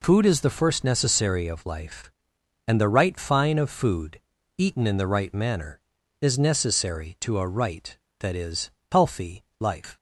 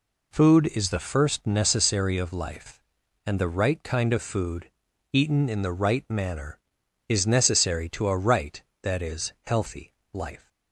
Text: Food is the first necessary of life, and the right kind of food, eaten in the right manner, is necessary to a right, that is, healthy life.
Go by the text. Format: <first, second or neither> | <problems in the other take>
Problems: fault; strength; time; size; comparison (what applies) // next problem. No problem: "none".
second | says "fine" for "kind"; at 3.1 s // pauses between "healthy" and "life"; slight; at 9.4 s; 0.16 s long; slight in the second